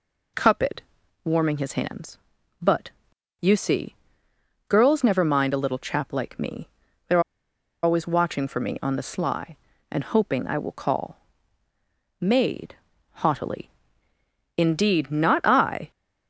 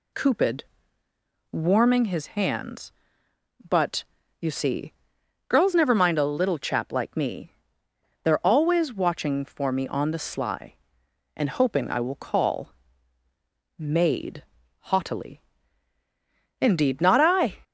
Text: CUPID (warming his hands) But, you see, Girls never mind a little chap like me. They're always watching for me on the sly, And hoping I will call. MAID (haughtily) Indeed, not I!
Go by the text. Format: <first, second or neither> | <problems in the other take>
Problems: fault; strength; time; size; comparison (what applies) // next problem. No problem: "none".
second | pauses between "They're" and "always"; noticeable; at 7.1 s; 0.63 s long